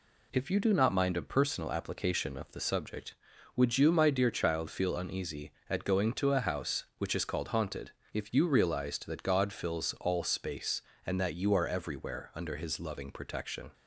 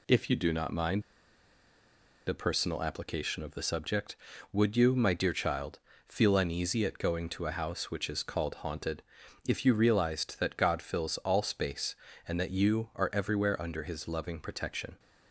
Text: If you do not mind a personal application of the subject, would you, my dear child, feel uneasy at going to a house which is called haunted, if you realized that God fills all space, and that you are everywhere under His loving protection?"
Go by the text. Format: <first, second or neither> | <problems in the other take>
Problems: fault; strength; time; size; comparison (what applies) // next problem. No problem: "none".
first | pauses between "mind" and "a"; strong; at 1.0 s; 1.2 s long